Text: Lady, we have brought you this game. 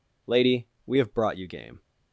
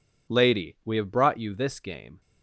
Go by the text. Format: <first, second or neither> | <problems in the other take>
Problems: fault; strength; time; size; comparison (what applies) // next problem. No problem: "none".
second | skips "this"; at 1.4 s